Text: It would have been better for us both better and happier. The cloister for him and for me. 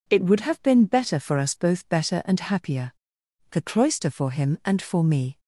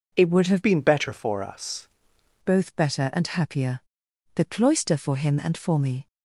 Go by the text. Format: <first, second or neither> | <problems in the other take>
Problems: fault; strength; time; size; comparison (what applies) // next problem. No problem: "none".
first | changes voice from "been" to "us"; from 0.6 to 1.8 s; 1.2 s long